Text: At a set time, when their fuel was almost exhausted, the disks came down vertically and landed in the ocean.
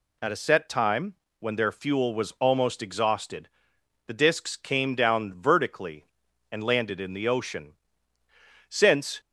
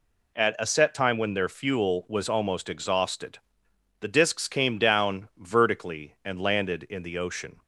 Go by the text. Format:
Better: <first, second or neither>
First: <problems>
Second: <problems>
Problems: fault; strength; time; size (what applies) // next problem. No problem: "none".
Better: second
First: goes on to say "Since"; from 8.6 s on; 0.52 s long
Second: none